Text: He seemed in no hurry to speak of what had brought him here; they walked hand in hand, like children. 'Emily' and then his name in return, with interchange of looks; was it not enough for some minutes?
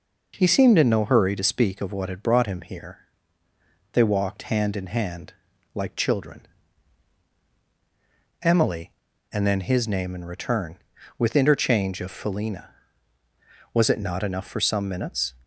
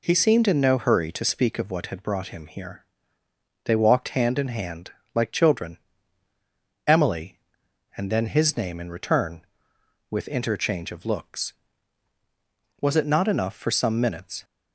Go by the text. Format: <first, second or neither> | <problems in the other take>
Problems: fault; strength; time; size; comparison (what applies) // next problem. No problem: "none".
second | says "felina" for "looks"; at 12.1 s